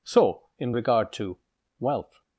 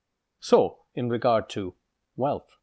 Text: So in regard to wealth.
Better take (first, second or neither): neither